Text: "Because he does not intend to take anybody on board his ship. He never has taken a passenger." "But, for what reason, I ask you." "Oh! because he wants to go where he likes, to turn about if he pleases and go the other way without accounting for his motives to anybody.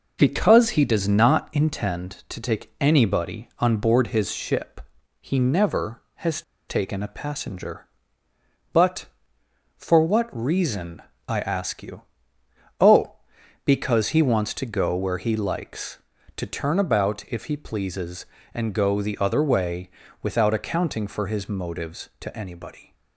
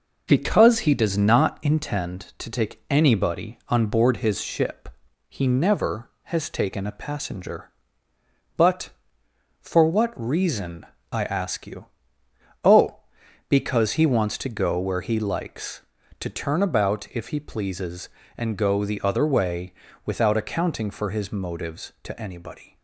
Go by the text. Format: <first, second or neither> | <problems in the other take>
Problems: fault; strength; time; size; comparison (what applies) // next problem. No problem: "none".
second | pauses between "has" and "taken"; slight; at 6.4 s; 0.27 s long // pauses between "way" and "without"; slight; at 19.8 s; 0.32 s long; slight in the second